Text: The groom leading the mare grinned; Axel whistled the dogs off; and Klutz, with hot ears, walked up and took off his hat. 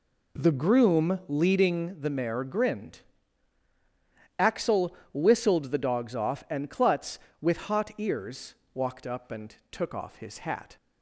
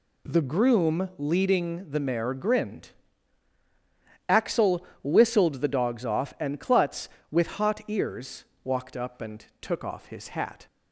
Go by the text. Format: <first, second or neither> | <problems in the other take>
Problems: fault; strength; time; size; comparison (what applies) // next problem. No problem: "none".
second | starts louder than the rest; slight; until 2.0 s; 3 dB // pauses between "Axel" and "whistled"; slight; at 4.9 s; 0.20 s long; slight in the second // pauses between "and" and "took"; slight; at 9.5 s; 0.16 s long; slight in the second